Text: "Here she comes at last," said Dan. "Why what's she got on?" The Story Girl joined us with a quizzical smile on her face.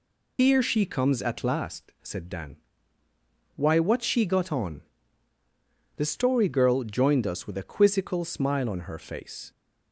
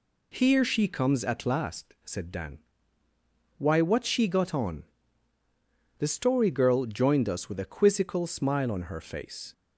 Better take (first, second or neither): second